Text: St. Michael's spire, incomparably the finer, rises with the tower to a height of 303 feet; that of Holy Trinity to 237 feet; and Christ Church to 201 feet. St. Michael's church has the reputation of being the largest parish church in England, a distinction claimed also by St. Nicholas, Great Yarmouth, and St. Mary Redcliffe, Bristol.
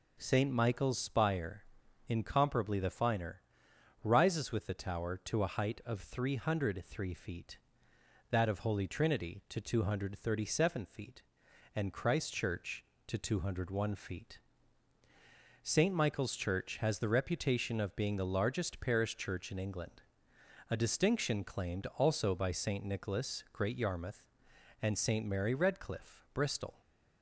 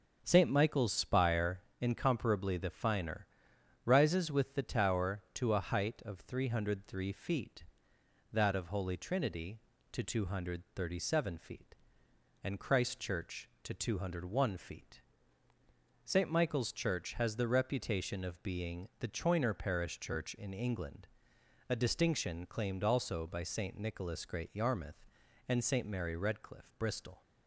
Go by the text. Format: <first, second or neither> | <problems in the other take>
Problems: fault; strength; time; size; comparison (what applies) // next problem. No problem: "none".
first | starts louder than the rest; until 1.2 s; 6.5 dB // says "choiner" for "largest"; at 19.0 s